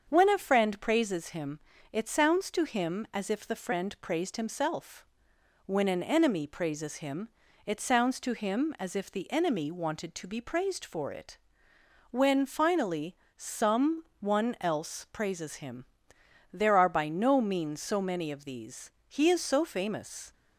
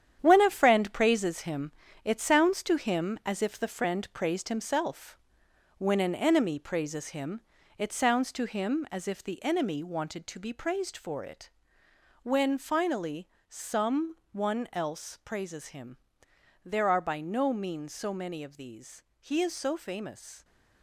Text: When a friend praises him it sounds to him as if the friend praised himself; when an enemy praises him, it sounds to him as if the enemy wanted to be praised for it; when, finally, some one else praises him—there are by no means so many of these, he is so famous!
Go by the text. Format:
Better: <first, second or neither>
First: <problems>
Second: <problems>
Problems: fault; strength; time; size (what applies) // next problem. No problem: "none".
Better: first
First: starts louder than the rest; until 1.1 s; 7 dB // pauses between "him" and "it"; slight; at 1.5 s; 0.34 s long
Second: gets quieter; strong; throughout; 9 dB // starts louder than the rest; strong; until 1.2 s; 9.5 dB // pauses between "him" and "it"; slight; at 1.7 s; 0.34 s long